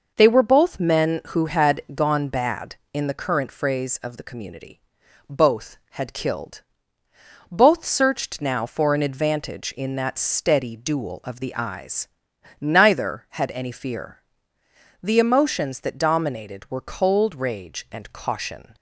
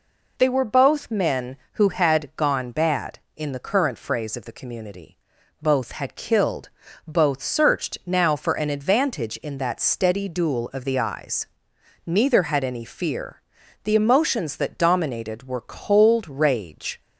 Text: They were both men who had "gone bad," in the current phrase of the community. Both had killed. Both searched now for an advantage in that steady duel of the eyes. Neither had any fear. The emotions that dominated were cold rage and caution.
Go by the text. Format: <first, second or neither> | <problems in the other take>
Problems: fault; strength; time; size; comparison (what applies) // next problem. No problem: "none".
first | stops before "and caution"; at 17.0 s